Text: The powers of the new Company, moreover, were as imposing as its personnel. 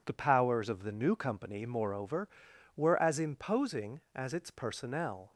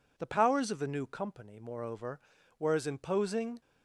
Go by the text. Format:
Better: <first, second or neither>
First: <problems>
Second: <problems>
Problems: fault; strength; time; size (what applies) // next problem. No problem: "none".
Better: first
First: none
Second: stops before "as its personnel"; at 3.6 s